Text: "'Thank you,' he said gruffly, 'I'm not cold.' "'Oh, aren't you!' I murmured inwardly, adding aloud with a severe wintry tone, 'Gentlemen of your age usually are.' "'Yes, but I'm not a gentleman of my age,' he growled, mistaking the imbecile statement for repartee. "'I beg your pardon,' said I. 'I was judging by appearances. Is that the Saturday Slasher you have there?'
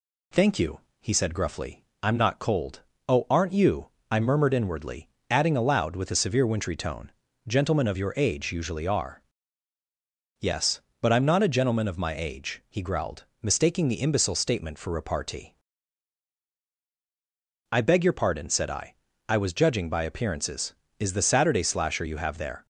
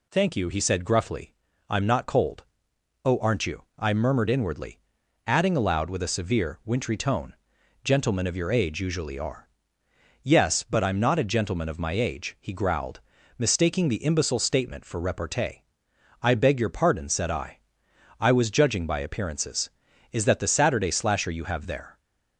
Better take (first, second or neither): second